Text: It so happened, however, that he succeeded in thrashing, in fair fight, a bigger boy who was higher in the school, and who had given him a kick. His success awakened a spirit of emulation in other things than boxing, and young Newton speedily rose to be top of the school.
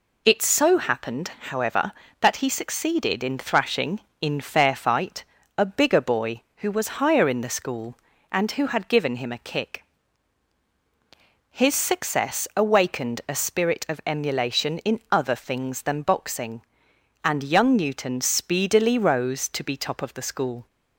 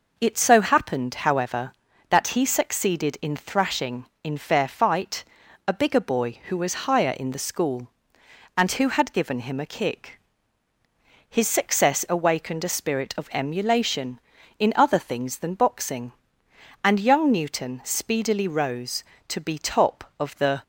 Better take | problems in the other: first | stops before "school"; at 20.6 s

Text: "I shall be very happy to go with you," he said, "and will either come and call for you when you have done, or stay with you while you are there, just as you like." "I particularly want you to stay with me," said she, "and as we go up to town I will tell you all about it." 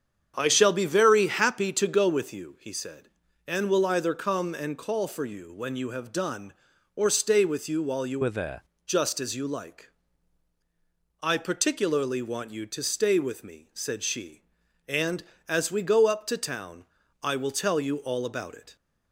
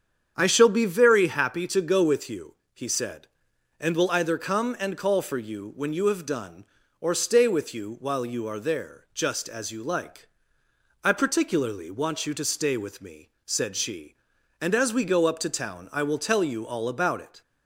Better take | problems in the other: second | starts louder than the rest; strong; until 1.3 s; 8 dB; strong in the second // changes voice from "are" to "there"; from 8.2 to 8.6 s; 0.4 s long // pauses between "town" and "I"; slight; at 16.8 s; 0.36 s long

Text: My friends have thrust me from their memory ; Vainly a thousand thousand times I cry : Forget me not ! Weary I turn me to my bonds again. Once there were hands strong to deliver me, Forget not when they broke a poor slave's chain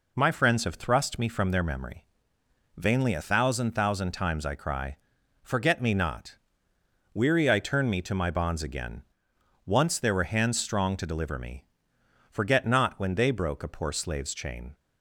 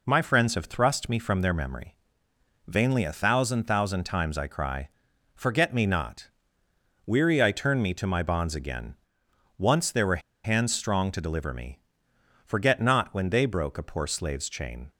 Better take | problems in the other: first | pauses between "were" and "hands"; slight; at 10.2 s; 0.22 s long

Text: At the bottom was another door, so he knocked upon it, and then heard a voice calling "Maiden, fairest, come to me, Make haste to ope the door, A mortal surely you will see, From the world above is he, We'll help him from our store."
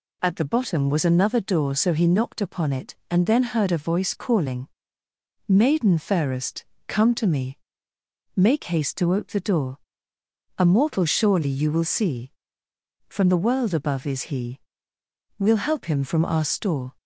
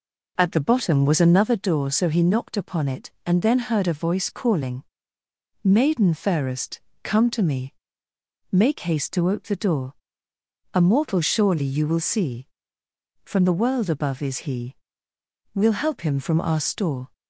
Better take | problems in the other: first | starts louder than the rest; noticeable; until 1.6 s; 4.5 dB // pauses between "calling" and "Maiden"; noticeable; at 4.8 s; 0.80 s long; noticeable in the first

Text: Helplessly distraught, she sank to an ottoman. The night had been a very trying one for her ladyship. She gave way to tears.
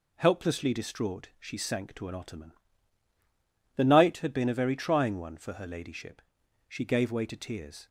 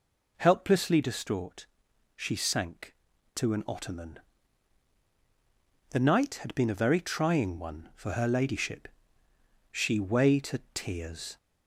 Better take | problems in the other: first | skips "gave"; at 9.9 s

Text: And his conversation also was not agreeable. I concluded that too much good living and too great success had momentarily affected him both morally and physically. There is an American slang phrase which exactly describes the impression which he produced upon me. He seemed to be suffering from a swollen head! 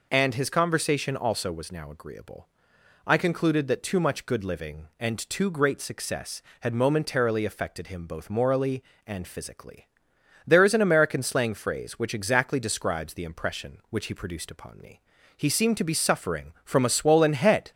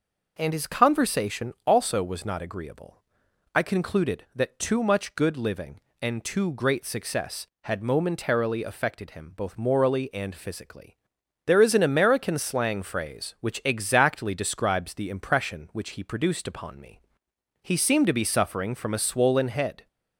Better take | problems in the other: second | says "now" for "not"; at 1.7 s

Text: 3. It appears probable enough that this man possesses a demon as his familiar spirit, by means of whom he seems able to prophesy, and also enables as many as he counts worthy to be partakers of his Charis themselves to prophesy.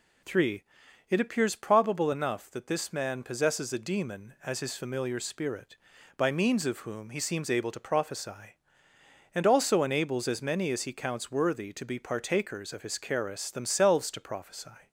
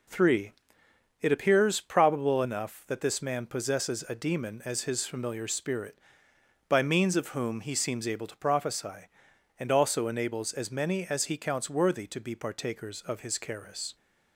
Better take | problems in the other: first | stops before "themselves to prophesy"; at 13.9 s

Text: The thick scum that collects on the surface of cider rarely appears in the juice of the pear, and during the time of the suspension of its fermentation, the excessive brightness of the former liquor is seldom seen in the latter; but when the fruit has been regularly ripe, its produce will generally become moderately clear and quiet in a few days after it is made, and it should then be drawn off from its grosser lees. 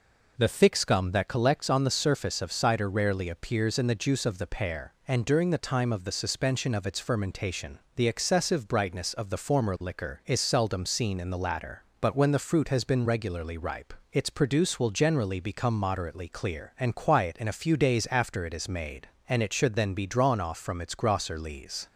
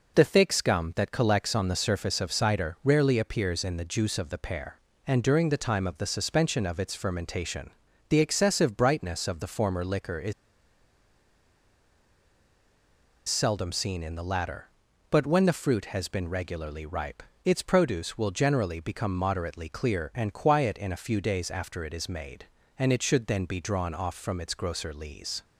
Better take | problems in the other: first | pauses between "is" and "seldom"; strong; at 10.3 s; 2.9 s long

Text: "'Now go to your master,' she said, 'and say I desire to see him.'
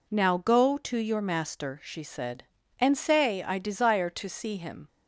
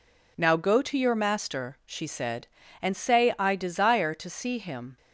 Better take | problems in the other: neither | none

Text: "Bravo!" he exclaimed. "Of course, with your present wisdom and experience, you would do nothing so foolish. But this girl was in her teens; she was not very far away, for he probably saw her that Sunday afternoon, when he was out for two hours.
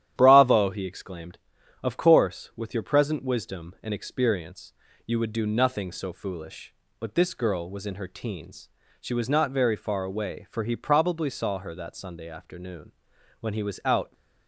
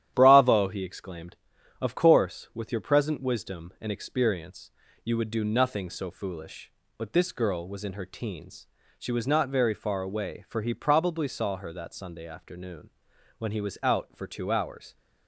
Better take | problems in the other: second | starts louder than the rest; strong; until 1.1 s; 11 dB; strong in the second // stops before "for two hours"; at 14.1 s

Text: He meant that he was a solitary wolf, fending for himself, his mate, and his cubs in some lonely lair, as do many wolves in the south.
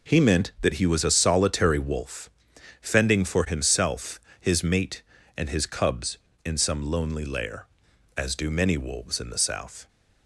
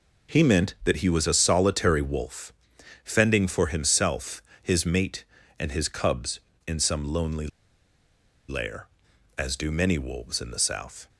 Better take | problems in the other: first | pauses between "lonely" and "lair"; at 7.4 s; 1.0 s long

